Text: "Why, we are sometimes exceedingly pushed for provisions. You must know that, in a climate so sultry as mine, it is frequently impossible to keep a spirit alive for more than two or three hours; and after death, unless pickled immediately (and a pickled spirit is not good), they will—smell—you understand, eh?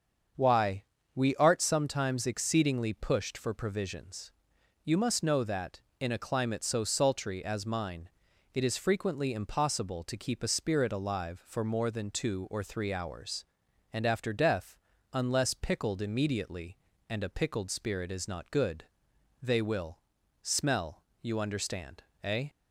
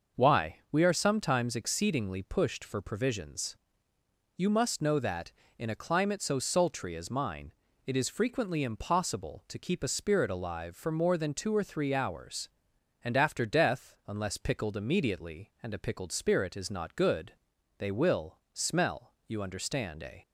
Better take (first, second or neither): second